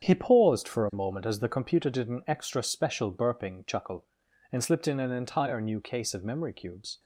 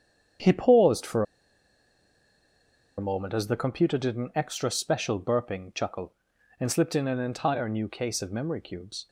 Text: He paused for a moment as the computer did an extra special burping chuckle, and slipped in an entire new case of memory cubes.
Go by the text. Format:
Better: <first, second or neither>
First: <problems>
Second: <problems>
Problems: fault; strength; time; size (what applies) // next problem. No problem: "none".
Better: first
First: starts louder than the rest; strong; until 1.0 s; 8 dB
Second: starts louder than the rest; strong; until 3.1 s; 8 dB // pauses between "for" and "a"; strong; at 1.2 s; 1.7 s long